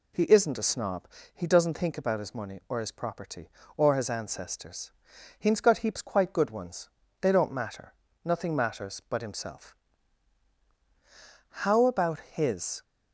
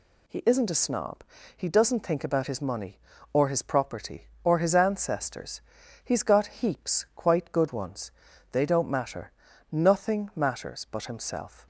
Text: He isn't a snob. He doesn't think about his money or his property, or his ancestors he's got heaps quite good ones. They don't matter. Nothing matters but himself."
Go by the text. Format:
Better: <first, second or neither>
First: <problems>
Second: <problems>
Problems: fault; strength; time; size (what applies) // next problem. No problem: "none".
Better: second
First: pauses between "ancestors" and "he's"; noticeable; at 4.9 s; 0.48 s long // goes on to say "How about his"; noticeable; from 11.6 s on; 1.2 s long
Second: pauses between "ancestors" and "he's"; at 5.6 s; 0.42 s long